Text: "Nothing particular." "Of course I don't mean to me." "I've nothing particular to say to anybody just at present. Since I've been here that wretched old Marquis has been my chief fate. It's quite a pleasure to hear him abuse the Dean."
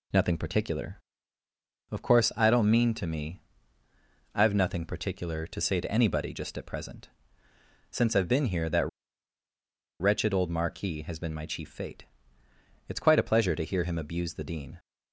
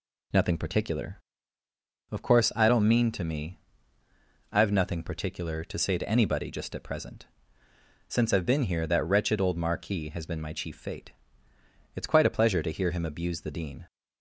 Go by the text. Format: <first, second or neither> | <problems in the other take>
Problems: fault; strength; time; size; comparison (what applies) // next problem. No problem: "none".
second | pauses between "that" and "wretched"; at 8.8 s; 1.1 s long